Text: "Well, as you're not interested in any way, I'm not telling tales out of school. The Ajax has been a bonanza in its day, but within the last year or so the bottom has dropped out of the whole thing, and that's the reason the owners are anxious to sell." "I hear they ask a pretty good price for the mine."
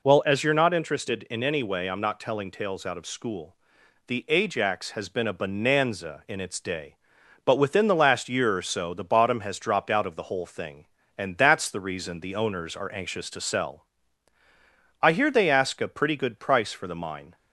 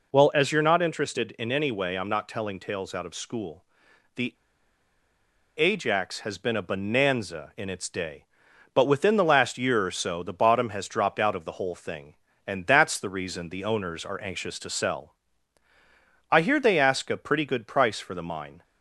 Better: first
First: none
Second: pauses between "The" and "Ajax"; at 4.3 s; 1.2 s long

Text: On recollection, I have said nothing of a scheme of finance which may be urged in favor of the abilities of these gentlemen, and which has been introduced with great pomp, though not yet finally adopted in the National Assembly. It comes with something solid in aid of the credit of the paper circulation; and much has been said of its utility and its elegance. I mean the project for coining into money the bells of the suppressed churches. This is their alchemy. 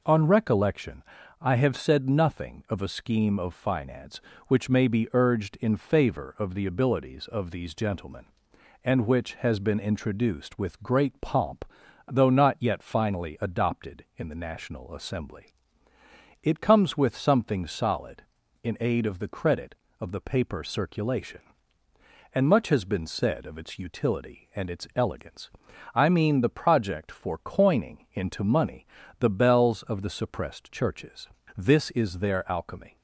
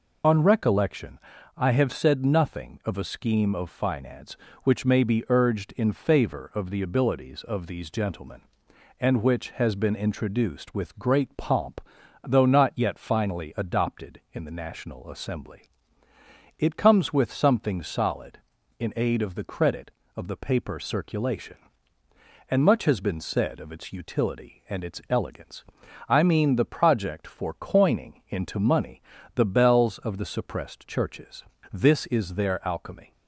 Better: first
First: pauses between "money" and "the"; slight; at 28.8 s; 0.32 s long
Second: loses the start of "On"; at 0.2 s; 50 ms // pauses between "money" and "the"; slight; at 29.0 s; 0.32 s long

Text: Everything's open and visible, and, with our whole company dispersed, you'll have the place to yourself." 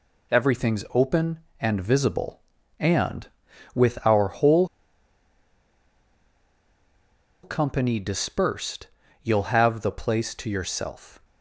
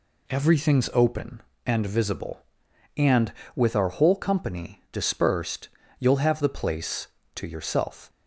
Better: second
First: pauses between "whole" and "company"; strong; at 4.6 s; 2.7 s long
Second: none

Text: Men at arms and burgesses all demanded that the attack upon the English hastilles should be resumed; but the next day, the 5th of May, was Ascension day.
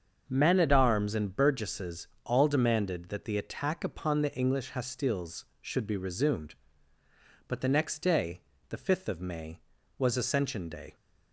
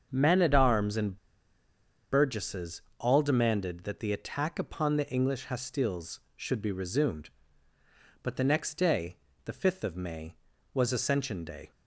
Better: first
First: starts louder than the rest; until 1.2 s; 7 dB // pauses between "burgesses" and "all"; slight; at 2.0 s; 0.16 s long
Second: starts louder than the rest; until 1.1 s; 7 dB // pauses between "and" and "burgesses"; noticeable; at 1.1 s; 0.92 s long // pauses between "burgesses" and "all"; slight; at 2.8 s; 0.16 s long

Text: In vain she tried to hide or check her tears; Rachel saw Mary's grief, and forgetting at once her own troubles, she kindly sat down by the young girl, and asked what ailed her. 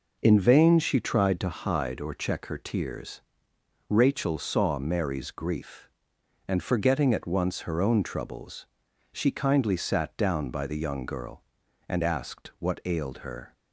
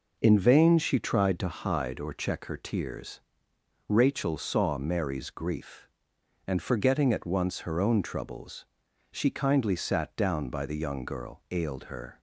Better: first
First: none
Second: skips "and asked what"; at 11.4 s

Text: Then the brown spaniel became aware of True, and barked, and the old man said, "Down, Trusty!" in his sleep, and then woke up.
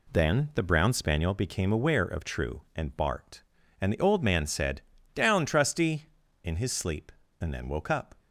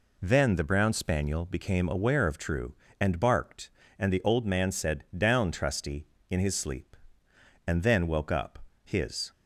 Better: first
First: none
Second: goes on to say "His"; slight; from 8.8 s on; 0.48 s long

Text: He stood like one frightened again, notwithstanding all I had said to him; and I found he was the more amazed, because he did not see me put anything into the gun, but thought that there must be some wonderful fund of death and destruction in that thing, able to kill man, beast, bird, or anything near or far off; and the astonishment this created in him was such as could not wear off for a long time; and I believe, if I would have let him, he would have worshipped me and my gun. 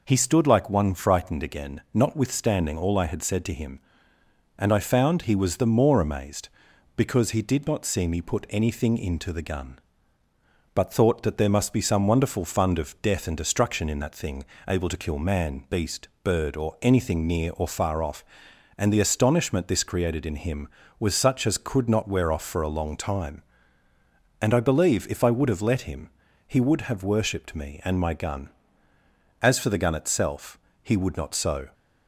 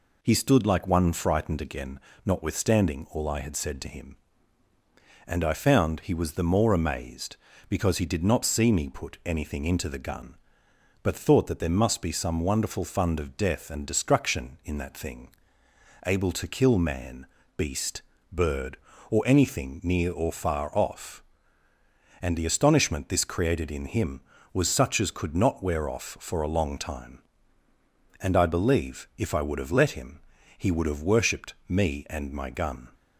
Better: second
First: goes on to say "As for the gun itself he would not so"; strong; from 29.4 s on; 2.3 s long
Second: none

